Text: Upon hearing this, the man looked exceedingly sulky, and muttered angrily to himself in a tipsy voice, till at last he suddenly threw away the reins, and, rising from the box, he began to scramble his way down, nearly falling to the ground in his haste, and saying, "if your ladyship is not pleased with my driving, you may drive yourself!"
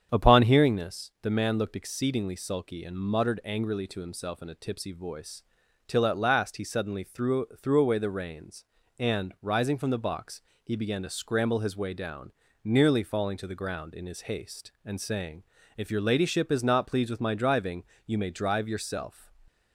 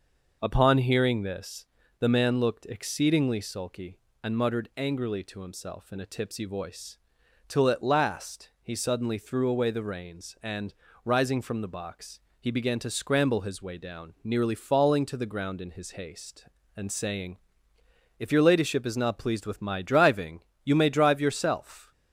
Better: second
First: starts louder than the rest; strong; until 1.1 s; 8 dB // says "threw" twice; at 7.6 s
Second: none

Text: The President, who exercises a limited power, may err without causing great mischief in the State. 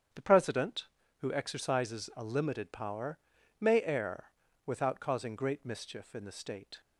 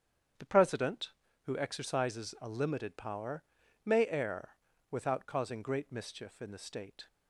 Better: neither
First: starts louder than the rest; strong; until 1.5 s; 8.5 dB // pauses between "err" and "without"; at 4.2 s; 0.42 s long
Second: starts louder than the rest; strong; until 1.7 s; 8.5 dB // pauses between "err" and "without"; at 4.4 s; 0.42 s long

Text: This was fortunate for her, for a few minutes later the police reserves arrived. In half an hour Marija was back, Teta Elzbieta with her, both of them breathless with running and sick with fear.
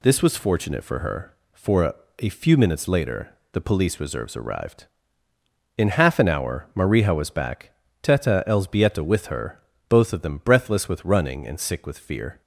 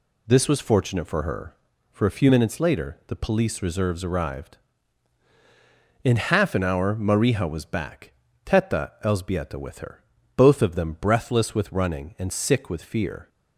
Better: second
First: says "a" twice; at 2.1 s // pauses between "later" and "the"; slight; at 3.3 s; 0.22 s long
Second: none

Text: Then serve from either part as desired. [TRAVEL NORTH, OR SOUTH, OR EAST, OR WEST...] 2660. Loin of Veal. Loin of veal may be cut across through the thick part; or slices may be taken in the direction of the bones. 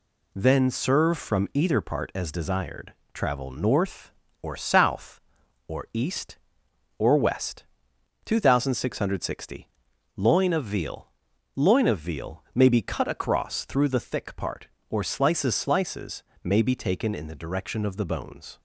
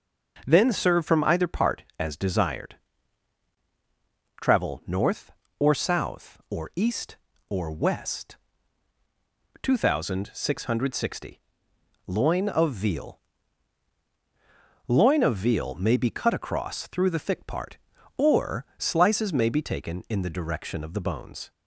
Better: second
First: says "slices" twice; at 15.5 s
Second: none

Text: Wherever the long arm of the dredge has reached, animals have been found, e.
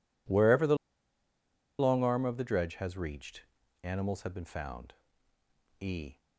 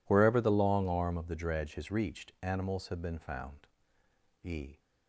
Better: second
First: pauses between "the" and "long"; at 0.7 s; 1.0 s long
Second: none

